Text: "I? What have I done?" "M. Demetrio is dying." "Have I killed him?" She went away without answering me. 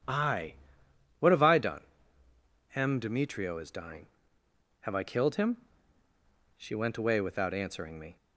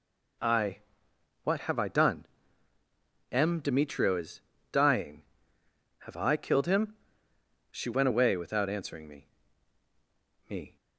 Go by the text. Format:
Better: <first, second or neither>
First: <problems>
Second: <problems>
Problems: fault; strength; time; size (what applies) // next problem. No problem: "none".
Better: first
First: none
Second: pauses between "is" and "dying"; slight; at 4.4 s; 0.28 s long // says "me" twice; at 10.4 s